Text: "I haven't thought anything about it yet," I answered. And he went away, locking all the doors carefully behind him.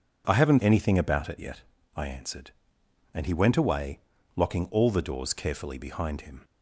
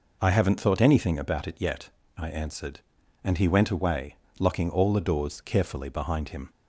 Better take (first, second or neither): second